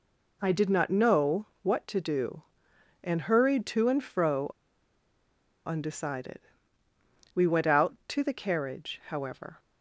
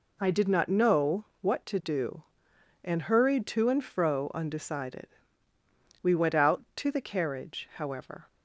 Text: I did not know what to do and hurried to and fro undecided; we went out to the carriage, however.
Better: second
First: pauses between "know" and "what"; slight; at 1.4 s; 0.16 s long // pauses between "fro" and "undecided"; at 4.4 s; 1.1 s long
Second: pauses between "know" and "what"; slight; at 1.2 s; 0.16 s long

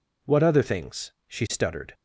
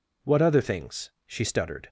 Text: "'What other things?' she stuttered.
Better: neither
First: none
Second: none

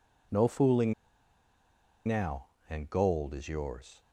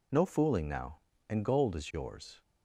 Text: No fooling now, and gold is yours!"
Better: second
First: pauses between "fooling" and "now"; at 0.9 s; 1.1 s long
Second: none

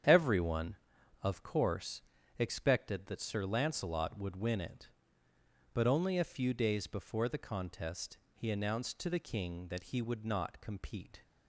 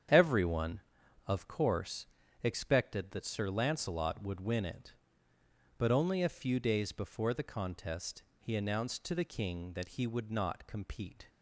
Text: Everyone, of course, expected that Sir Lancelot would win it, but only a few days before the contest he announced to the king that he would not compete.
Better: neither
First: starts louder than the rest; strong; until 1.5 s; 8.5 dB // pauses between "contest" and "he"; slight; at 8.1 s; 0.16 s long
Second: starts louder than the rest; strong; until 1.6 s; 8.5 dB // pauses between "contest" and "he"; slight; at 8.2 s; 0.16 s long

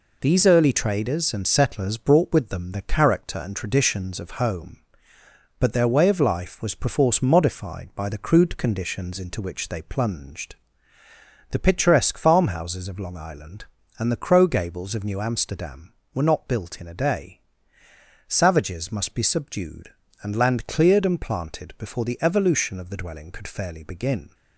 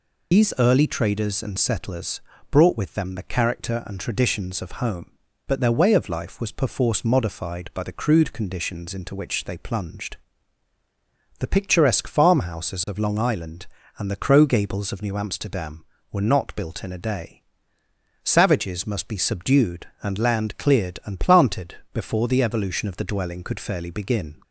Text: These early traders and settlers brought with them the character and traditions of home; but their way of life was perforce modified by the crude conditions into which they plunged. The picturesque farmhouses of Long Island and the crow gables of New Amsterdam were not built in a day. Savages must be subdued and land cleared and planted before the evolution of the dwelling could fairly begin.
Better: first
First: none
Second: loses the start of "These"; at 0.3 s; 80 ms // pauses between "settlers" and "brought"; slight; at 2.2 s; 0.30 s long // pauses between "planted" and "before"; slight; at 21.7 s; 0.16 s long

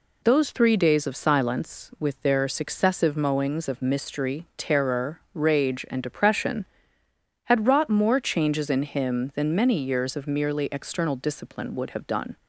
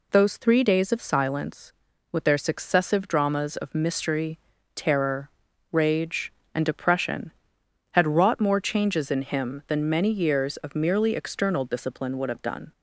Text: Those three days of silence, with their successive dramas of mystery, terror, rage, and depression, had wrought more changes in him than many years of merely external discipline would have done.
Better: second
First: says "mowings" for "dramas"; at 3.1 s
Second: none

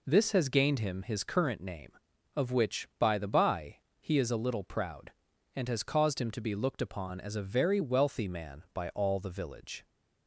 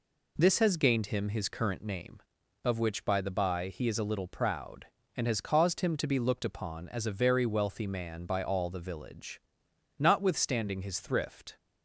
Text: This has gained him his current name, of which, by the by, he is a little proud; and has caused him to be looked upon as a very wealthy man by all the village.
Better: first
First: none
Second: goes on to say "Notwithstanding his thrift"; from 9.9 s on; 1.6 s long

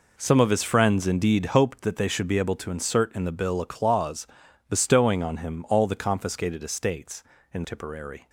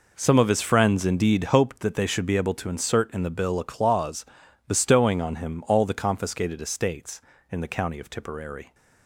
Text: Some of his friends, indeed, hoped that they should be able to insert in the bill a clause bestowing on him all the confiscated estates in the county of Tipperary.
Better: second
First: pauses between "clause" and "bestowing"; at 4.2 s; 0.42 s long // skips "the county of"; at 7.6 s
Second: pauses between "clause" and "bestowing"; at 4.2 s; 0.42 s long

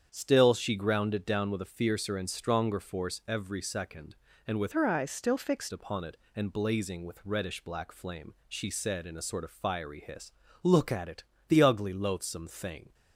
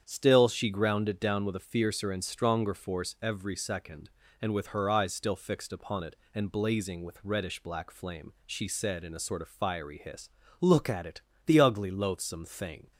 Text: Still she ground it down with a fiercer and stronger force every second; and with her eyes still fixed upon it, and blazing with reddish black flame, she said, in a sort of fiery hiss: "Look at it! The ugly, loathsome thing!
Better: second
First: starts louder than the rest; strong; until 1.1 s; 8 dB // changes voice from "her" to "fixed"; from 4.7 to 5.7 s; 1.0 s long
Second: starts louder than the rest; strong; until 1.0 s; 8 dB

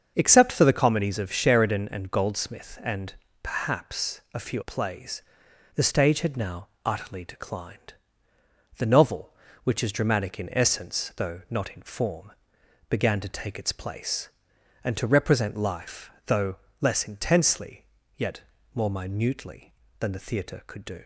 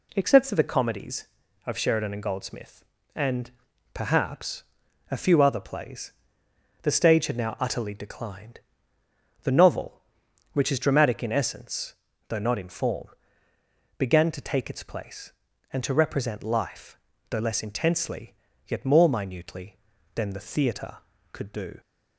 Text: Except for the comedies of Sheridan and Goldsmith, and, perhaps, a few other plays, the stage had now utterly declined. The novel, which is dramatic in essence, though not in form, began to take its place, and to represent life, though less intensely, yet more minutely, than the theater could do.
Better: second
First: starts louder than the rest; until 1.1 s; 7 dB // skips "other"; at 4.6 s // pauses between "now" and "utterly"; slight; at 6.6 s; 0.18 s long // pauses between "though" and "less"; slight; at 16.5 s; 0.24 s long // pauses between "yet" and "more"; slight; at 18.3 s; 0.34 s long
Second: none

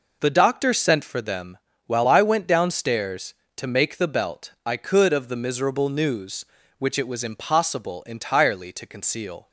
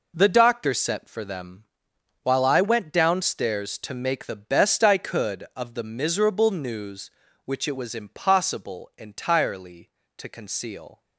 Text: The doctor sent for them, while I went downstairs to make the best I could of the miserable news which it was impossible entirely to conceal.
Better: second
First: says "belt" for "best"; at 4.0 s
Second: none

